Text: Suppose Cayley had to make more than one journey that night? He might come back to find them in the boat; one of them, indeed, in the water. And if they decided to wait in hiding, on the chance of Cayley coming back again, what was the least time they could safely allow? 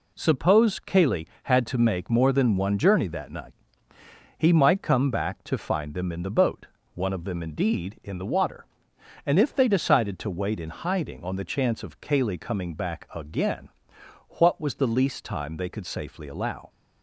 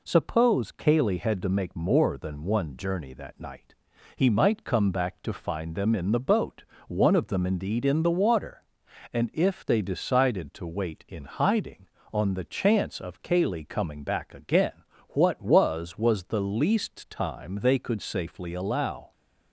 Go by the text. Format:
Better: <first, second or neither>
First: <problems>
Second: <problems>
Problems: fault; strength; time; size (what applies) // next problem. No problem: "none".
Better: first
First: none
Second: says "was" twice; at 15.9 s